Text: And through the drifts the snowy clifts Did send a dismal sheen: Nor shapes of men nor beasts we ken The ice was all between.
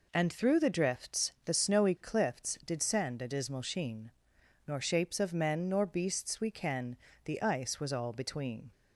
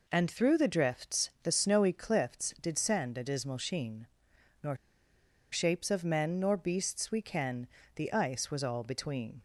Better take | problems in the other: first | pauses between "Nor" and "shapes"; noticeable; at 4.7 s; 0.75 s long // pauses between "ken" and "The"; slight; at 7.6 s; 0.26 s long; slight in the first

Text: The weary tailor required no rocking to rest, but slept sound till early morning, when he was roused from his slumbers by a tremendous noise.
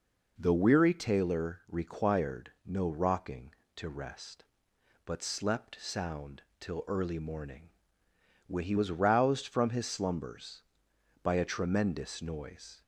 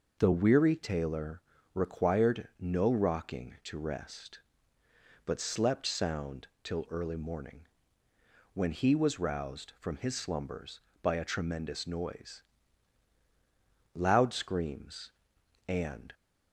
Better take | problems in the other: first | pauses between "tailor" and "required"; slight; at 1.4 s; 0.32 s long // pauses between "sound" and "till"; slight; at 6.4 s; 0.16 s long; slight in the first // goes on to say "Loud screams and"; strong; from 13.9 s on; 2.2 s long

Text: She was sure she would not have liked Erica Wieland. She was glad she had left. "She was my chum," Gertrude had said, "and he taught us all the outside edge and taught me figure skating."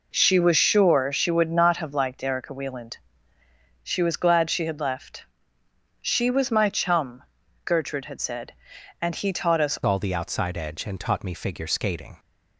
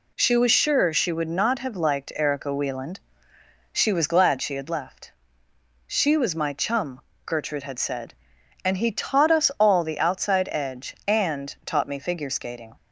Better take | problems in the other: second | changes voice at "all"; from 9.8 s on; 2.3 s long

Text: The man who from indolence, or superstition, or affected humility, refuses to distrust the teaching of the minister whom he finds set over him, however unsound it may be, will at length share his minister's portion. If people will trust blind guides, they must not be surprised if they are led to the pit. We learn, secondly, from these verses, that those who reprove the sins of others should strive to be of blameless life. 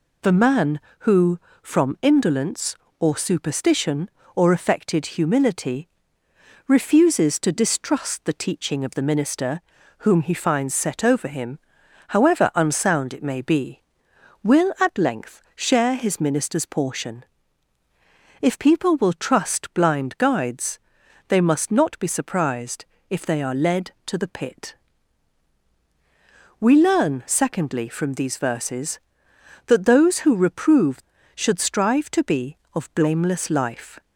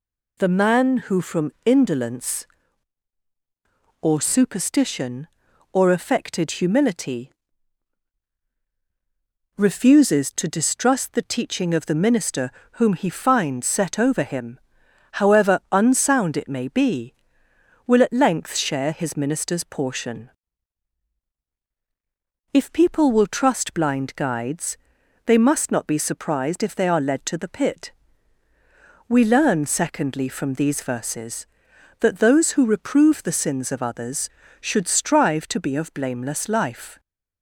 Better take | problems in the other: second | pauses between "minister" and "whom"; at 9.6 s; 0.38 s long; slight in the second // pauses between "surprised" and "if"; slight; at 22.8 s; 0.26 s long // skips "the sins of others"; at 31.1 s

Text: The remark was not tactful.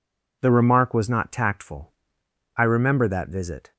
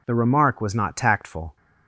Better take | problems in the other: second | goes on to say "I remember that visit"; noticeable; from 2.5 s on; 1.1 s long

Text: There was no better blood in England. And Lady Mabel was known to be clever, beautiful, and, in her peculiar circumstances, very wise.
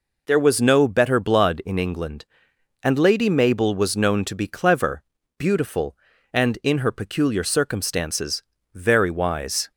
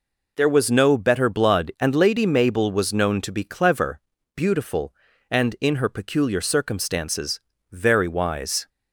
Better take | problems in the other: first | skips "in England"; at 1.7 s

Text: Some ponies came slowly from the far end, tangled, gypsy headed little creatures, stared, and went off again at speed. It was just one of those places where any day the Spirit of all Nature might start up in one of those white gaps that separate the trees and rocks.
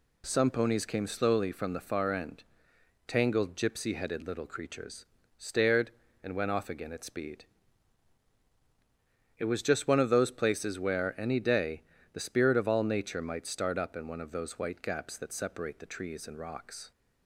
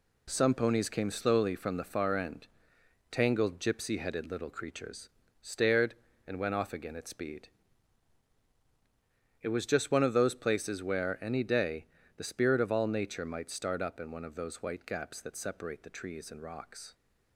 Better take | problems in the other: first | gets quieter; throughout; 7 dB // pauses between "day" and "the"; slight; at 11.8 s; 0.30 s long; slight in the first

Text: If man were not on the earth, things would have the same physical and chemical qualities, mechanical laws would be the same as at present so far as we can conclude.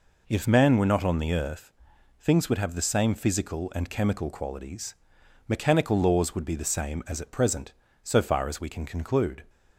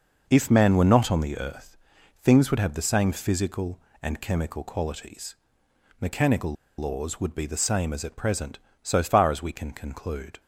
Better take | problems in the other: first | pauses between "mechanical" and "laws"; slight; at 6.5 s; 0.25 s long

